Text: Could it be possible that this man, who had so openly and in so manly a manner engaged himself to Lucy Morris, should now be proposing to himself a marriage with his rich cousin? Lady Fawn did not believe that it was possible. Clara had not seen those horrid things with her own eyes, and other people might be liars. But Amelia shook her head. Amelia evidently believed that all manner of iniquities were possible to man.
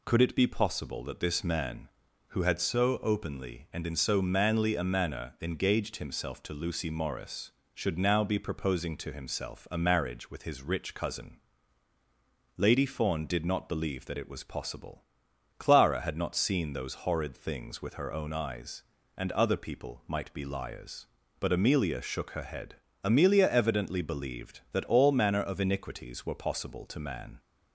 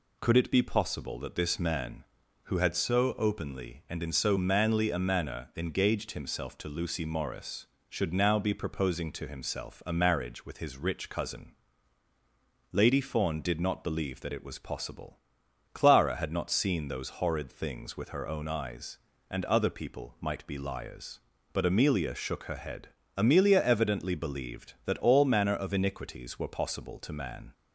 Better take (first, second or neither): neither